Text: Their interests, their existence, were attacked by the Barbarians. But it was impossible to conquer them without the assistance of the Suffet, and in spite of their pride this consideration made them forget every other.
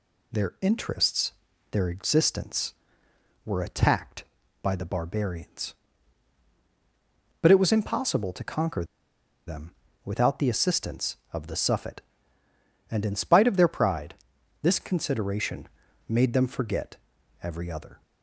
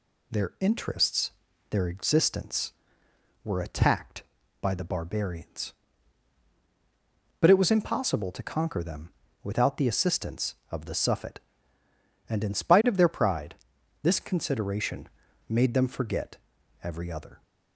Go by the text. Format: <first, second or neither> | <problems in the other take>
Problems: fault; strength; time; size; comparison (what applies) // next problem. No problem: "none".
second | pauses between "conquer" and "them"; noticeable; at 8.8 s; 0.63 s long // pauses between "them" and "without"; slight; at 9.7 s; 0.34 s long; slight in the second // pauses between "pride" and "this"; noticeable; at 14.1 s; 0.46 s long; noticeable in the second // pauses between "consideration" and "made"; at 15.6 s; 0.42 s long; also in the second // pauses between "forget" and "every"; noticeable; at 16.9 s; 0.46 s long; noticeable in the second